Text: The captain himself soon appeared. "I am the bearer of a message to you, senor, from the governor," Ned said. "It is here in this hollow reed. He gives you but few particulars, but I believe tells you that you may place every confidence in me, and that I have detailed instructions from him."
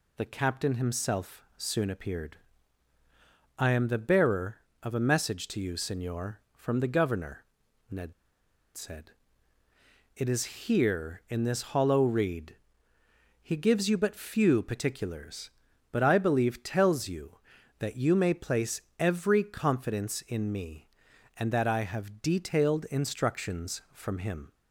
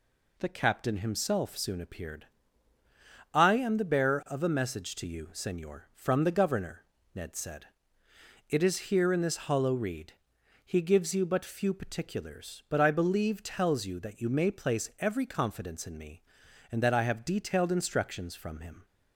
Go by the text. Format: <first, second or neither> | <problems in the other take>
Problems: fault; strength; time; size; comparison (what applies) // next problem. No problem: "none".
second | pauses between "Ned" and "said"; noticeable; at 8.1 s; 0.62 s long // pauses between "place" and "every"; slight; at 18.8 s; 0.16 s long